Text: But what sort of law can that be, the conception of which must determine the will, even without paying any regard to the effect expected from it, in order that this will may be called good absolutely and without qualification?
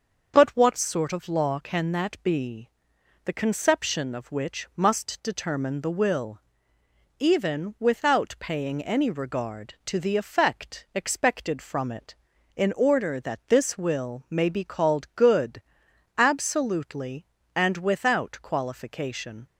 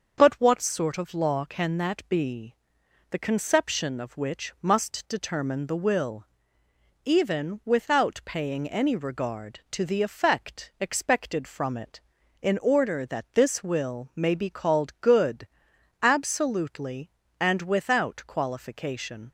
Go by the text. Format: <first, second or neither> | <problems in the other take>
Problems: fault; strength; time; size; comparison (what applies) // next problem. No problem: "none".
neither | starts louder than the rest; the same in both // pauses between "good" and "absolutely"; noticeable; the same in both